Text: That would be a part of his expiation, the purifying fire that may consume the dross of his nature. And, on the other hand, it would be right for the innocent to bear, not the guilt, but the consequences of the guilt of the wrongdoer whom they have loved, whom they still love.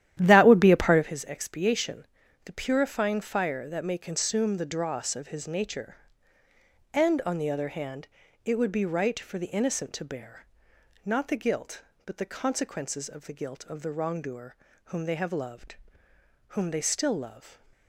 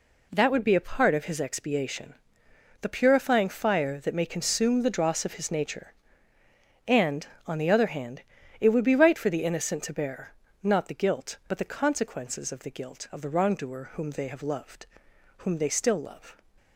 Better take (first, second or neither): second